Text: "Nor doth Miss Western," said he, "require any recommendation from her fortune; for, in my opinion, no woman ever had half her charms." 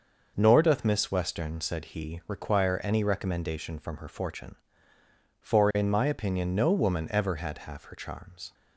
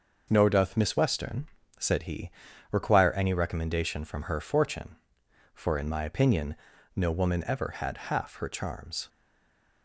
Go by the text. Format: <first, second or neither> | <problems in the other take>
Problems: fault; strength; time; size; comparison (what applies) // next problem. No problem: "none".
first | stays silent after the last word; slight; from 9.0 s on; 0.8 s long